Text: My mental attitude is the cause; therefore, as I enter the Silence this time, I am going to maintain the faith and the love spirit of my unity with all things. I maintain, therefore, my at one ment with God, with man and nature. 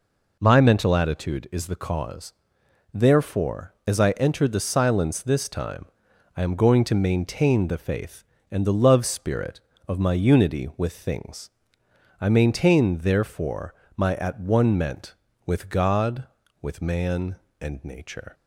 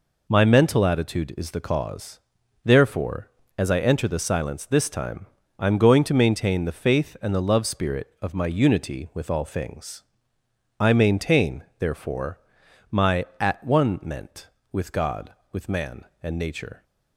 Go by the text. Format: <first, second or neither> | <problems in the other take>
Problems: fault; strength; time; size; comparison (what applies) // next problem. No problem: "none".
second | skips "all"; at 10.9 s